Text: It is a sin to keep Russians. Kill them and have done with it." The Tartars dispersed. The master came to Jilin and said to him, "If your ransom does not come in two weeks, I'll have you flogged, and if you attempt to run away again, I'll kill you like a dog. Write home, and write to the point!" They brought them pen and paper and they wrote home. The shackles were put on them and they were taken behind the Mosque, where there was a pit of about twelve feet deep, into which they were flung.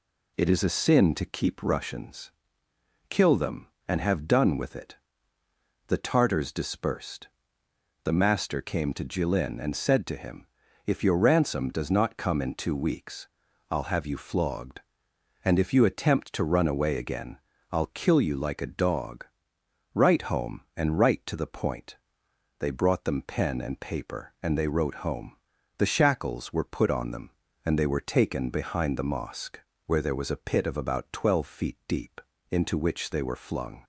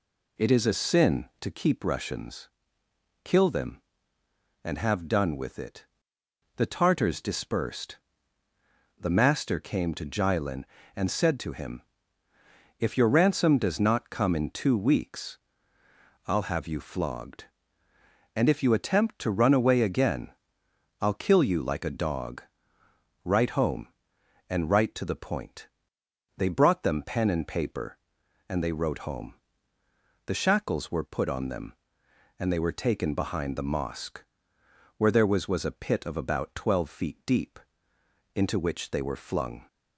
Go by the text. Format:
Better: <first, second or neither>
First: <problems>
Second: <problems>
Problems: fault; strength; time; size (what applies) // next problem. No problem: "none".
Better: first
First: none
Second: says "was" twice; at 35.4 s